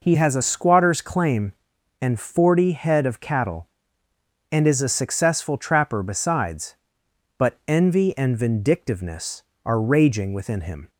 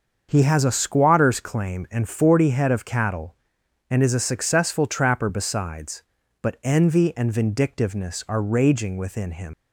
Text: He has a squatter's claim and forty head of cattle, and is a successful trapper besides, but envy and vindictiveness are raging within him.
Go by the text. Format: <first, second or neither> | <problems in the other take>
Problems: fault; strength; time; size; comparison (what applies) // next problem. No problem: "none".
first | starts louder than the rest; until 1.3 s; 6.5 dB // leaves "him" unfinished; at 9.5 s; 95 ms